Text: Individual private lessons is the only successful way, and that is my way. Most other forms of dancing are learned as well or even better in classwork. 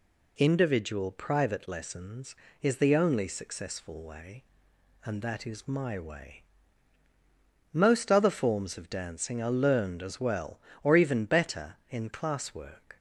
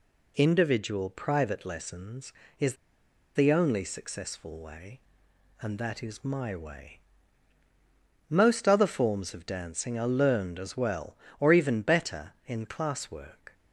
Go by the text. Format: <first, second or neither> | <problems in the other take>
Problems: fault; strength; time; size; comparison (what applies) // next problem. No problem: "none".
first | pauses between "is" and "the"; noticeable; at 2.7 s; 0.61 s long